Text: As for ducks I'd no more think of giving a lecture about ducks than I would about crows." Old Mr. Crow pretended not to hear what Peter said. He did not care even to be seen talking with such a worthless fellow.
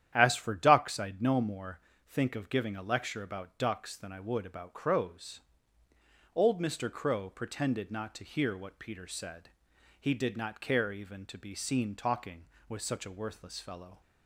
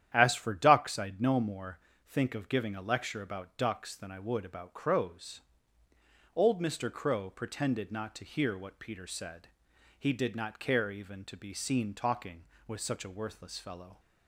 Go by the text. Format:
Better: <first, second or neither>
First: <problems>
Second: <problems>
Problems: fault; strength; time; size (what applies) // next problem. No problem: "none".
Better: neither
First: starts louder than the rest; strong; until 1.1 s; 10.5 dB // pauses between "more" and "think"; slight; at 1.7 s; 0.28 s long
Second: starts louder than the rest; strong; until 1.1 s; 10.5 dB // pauses between "more" and "think"; slight; at 1.7 s; 0.28 s long